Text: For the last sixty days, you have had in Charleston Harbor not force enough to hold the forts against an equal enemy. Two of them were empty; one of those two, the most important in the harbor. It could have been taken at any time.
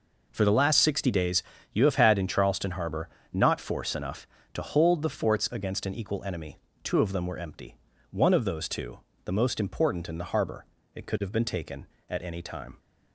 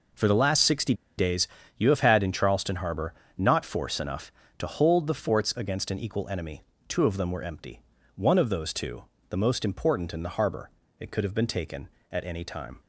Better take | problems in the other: first | pauses between "sixty" and "days"; slight; at 0.9 s; 0.24 s long // pauses between "Harbor" and "not"; slight; at 3.1 s; 0.24 s long; slight in the first

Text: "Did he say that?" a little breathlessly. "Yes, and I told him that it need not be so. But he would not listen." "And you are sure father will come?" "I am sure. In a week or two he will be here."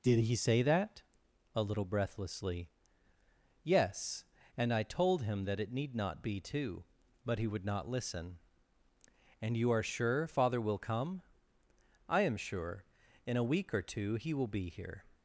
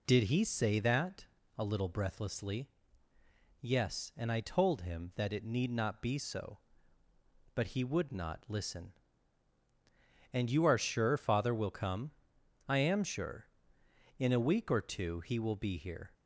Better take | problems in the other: second | says "too" for "so"; at 6.3 s

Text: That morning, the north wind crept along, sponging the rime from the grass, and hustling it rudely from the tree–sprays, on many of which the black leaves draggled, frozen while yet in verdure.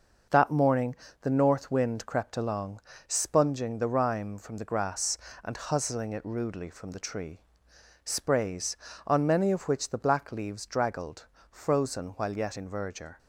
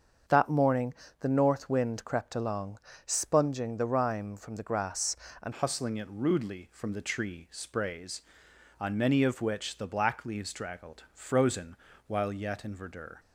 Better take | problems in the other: first | starts louder than the rest; strong; until 1.5 s; 7 dB; also in the first // changes voice at "hustling"; from 5.5 s on; 7.6 s long // pauses between "frozen" and "while"; slight; at 11.7 s; 0.32 s long

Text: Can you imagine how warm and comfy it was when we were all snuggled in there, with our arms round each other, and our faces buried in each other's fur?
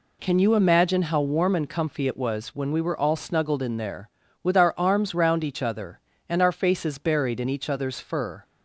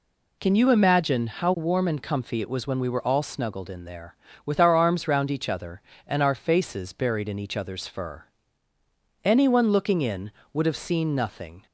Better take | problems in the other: first | goes on to say "Anyone looking in would have seen nothing"; strong; from 9.2 s on; 2.4 s long

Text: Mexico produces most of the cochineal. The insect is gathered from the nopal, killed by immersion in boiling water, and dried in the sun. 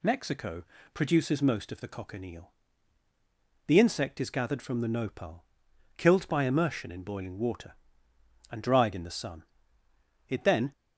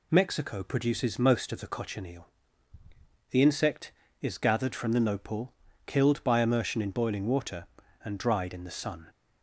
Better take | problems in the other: second | pauses between "Mexico" and "produces"; slight; at 0.6 s; 0.30 s long // goes on to say "It then"; slight; from 10.2 s on; 0.44 s long

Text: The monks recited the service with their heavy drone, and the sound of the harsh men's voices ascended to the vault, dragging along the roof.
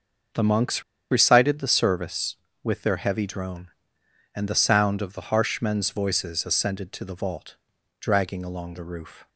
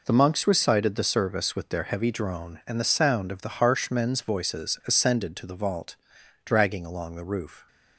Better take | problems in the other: second | starts louder than the rest; noticeable; until 1.6 s; 6 dB // pauses between "monks" and "recited"; slight; at 0.8 s; 0.29 s long

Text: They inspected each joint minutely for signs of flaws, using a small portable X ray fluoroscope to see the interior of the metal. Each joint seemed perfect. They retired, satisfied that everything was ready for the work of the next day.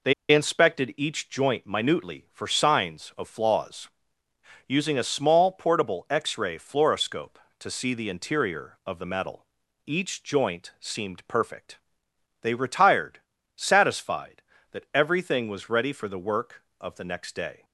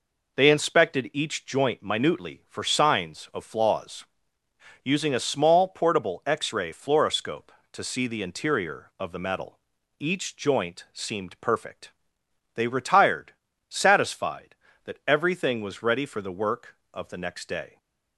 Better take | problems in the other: second | pauses between "They" and "inspected"; slight; at 0.1 s; 0.18 s long

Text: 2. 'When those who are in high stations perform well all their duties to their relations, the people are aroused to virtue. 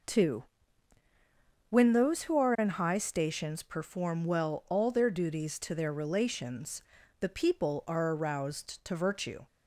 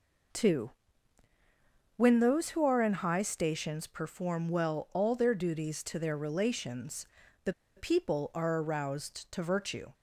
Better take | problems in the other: first | pauses between "the" and "people"; slight; at 7.5 s; 0.24 s long

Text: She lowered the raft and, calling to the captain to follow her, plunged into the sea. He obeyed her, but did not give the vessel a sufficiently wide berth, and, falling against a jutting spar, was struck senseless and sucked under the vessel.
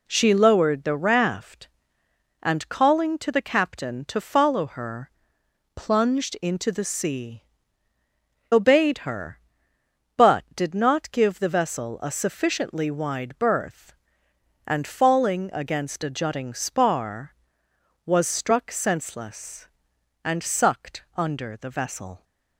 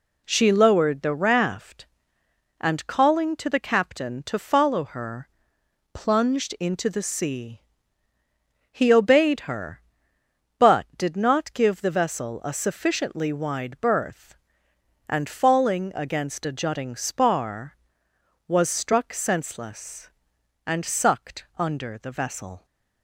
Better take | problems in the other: second | skips "He"; at 7.9 s // pauses between "sucked" and "under"; slight; at 21.0 s; 0.16 s long; slight in the second

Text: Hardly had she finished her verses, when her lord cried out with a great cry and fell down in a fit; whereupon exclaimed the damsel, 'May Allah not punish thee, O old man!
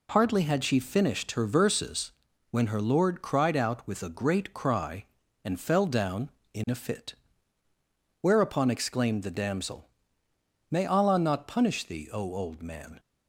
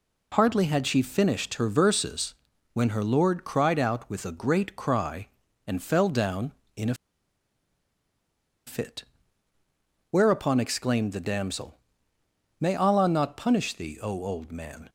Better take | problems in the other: first | pauses between "a" and "fit"; strong; at 6.9 s; 1.7 s long

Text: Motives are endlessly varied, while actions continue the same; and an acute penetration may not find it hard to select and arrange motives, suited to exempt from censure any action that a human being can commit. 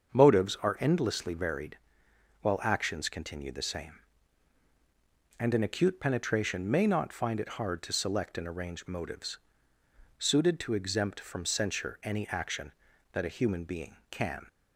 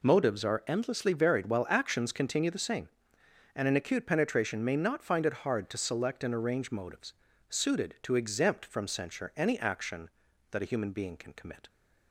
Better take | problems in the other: second | starts louder than the rest; until 1.2 s; 6.5 dB // stops before "commit"; at 14.4 s

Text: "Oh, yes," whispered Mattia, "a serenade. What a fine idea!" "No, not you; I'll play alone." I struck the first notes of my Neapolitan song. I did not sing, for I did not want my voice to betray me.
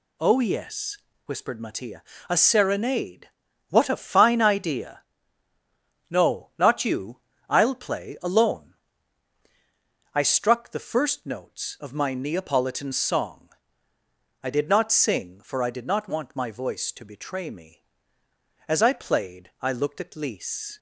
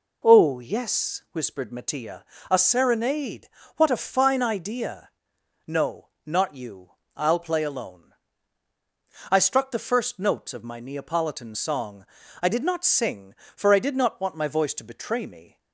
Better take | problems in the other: second | goes on to say "As I played I looked at Lise"; strong; from 18.6 s on; 2.1 s long

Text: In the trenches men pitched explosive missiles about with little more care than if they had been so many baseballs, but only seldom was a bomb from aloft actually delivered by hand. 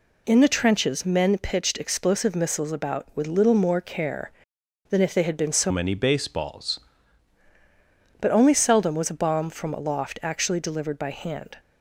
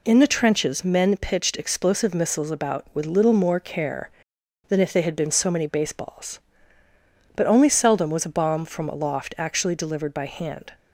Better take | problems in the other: second | changes voice from "many" to "baseballs"; from 5.7 to 6.8 s; 1.1 s long

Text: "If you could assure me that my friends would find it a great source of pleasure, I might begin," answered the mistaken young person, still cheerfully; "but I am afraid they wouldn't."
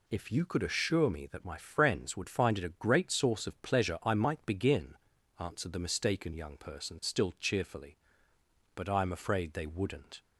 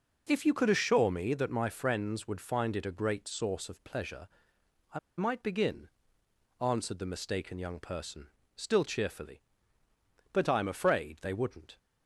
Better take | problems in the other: first | pauses between "I" and "might"; slight; at 4.9 s; 0.18 s long

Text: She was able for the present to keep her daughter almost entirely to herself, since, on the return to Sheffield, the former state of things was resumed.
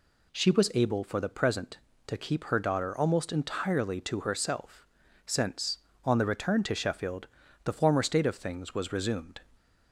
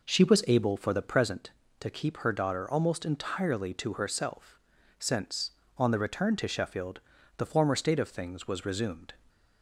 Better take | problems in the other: first | starts louder than the rest; noticeable; until 1.5 s; 4.5 dB

